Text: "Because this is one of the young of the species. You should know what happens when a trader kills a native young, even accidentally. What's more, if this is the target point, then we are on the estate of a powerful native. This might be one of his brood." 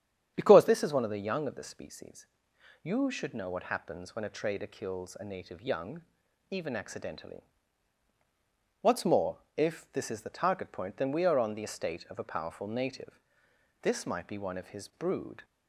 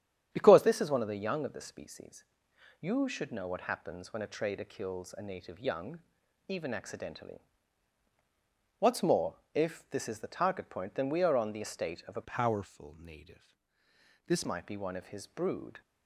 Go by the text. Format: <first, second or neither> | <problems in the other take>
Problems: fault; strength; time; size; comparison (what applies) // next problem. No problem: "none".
first | starts louder than the rest; strong; until 1.3 s; 9.5 dB; strong in the first // changes voice from "powerful" to "This"; from 12.2 to 14.4 s; 2.2 s long